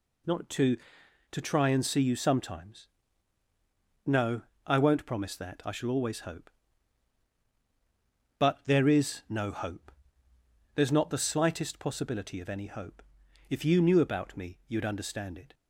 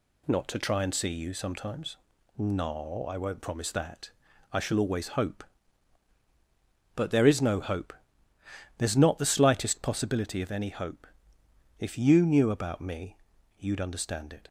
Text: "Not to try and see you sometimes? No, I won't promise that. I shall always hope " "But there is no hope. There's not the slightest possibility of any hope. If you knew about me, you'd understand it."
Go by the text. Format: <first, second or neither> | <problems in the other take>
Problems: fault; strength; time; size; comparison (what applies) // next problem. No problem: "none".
second | says "to" twice; at 1.3 s